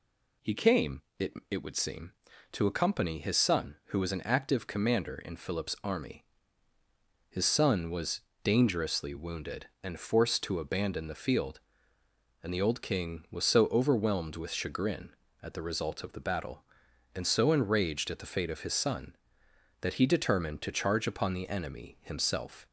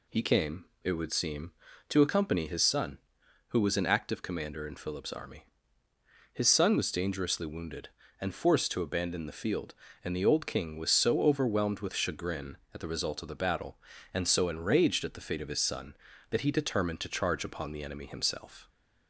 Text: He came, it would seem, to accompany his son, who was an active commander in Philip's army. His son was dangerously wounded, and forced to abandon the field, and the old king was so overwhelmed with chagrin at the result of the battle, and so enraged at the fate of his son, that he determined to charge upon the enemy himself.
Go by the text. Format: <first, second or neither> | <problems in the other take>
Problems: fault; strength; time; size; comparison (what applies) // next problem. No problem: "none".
second | says "it" twice; at 1.5 s // pauses between "was" and "dangerously"; slight; at 8.2 s; 0.22 s long